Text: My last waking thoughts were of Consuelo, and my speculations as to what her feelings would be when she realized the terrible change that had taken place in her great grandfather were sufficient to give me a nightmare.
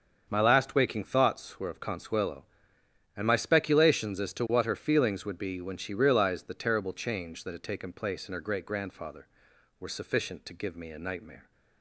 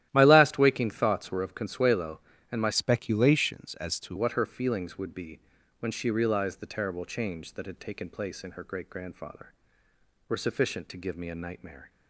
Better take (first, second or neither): first